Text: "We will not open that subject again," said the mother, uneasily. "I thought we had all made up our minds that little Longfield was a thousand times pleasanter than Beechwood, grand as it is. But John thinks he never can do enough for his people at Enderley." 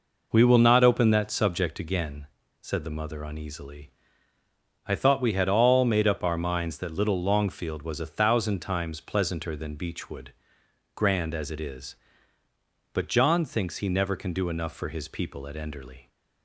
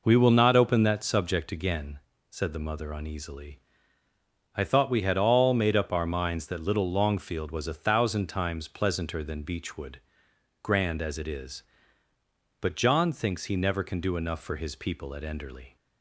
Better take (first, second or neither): neither